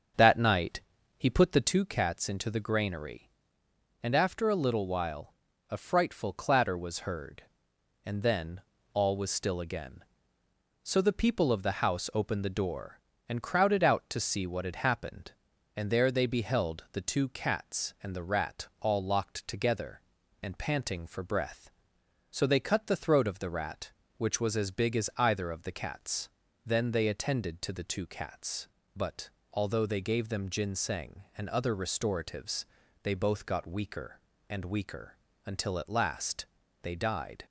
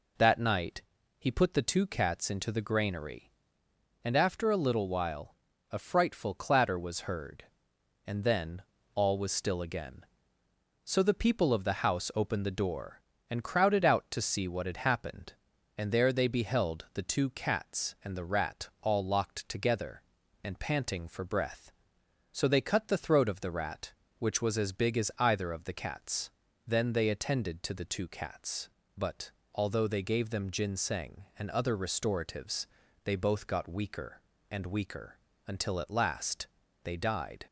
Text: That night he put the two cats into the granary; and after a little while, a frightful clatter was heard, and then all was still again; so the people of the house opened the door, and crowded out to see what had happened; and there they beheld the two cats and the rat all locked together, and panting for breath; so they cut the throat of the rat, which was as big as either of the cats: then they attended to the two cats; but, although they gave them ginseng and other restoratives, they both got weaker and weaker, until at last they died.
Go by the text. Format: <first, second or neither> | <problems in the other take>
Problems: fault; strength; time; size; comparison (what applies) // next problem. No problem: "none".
second | starts louder than the rest; until 1.8 s; 7 dB // pauses between "night" and "he"; slight; at 0.8 s; 0.36 s long; slight in the second // pauses between "then" and "all"; slight; at 8.6 s; 0.32 s long; slight in the second // pauses between "last" and "they"; slight; at 36.4 s; 0.36 s long; slight in the second